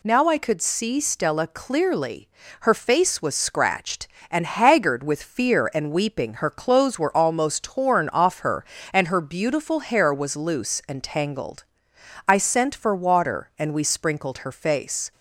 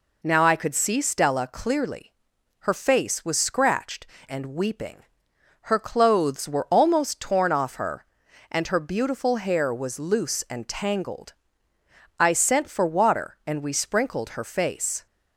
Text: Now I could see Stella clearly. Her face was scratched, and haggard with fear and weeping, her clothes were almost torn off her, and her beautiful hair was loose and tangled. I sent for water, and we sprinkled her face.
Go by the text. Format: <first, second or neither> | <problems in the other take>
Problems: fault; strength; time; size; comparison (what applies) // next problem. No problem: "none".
first | skips "and haggard with fear"; at 4.1 s